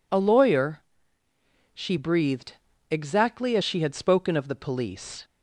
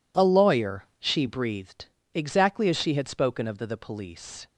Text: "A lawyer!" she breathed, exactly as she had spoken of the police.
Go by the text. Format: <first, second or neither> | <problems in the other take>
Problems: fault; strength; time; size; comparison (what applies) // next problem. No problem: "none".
first | says "the" twice; at 3.6 s